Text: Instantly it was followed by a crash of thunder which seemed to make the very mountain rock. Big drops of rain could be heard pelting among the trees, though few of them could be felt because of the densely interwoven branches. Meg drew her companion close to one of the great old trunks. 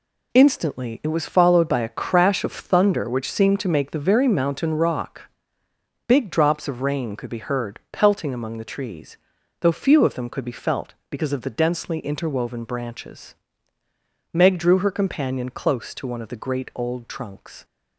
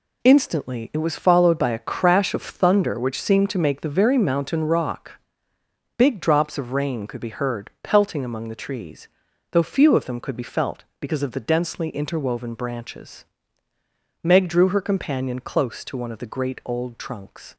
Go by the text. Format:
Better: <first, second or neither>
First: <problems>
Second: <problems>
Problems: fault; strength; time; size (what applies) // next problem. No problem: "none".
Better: neither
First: none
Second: none